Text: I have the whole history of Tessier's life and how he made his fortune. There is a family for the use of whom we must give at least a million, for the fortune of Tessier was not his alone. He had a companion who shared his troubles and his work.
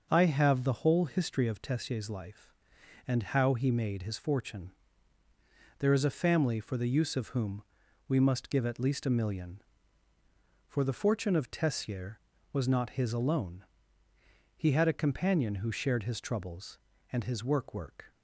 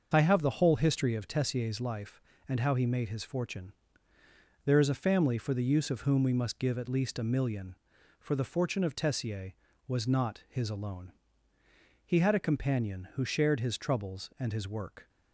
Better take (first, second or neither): second